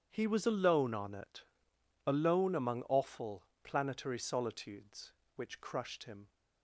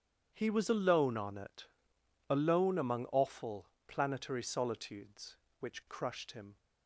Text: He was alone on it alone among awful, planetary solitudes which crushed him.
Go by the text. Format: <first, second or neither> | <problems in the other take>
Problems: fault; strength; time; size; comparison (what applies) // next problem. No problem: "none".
neither | starts louder than the rest; strong; the same in both // pauses between "it" and "alone"; noticeable; the same in both